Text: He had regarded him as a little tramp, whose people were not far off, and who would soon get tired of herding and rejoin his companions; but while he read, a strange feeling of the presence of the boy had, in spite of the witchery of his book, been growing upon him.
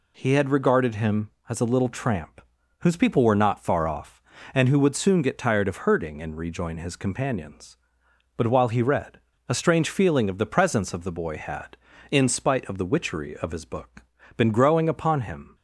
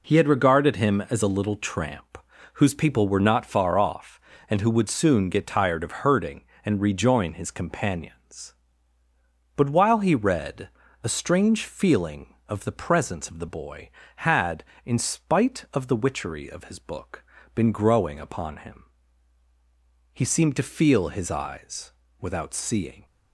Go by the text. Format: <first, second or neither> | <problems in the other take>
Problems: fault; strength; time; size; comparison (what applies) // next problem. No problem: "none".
first | goes on to say "He seemed to feel his eyes without seeing"; strong; from 20.1 s on; 2.9 s long